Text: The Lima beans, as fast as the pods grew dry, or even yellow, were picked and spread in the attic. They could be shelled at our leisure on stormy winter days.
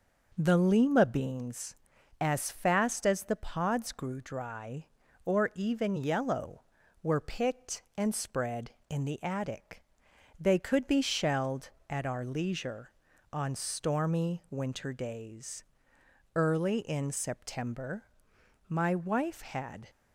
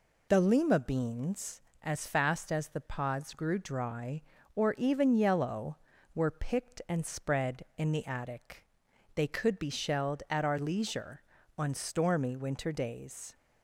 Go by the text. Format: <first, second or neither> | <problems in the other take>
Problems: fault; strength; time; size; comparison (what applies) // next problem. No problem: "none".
second | goes on to say "Early in September my wife had"; strong; from 16.3 s on; 3.5 s long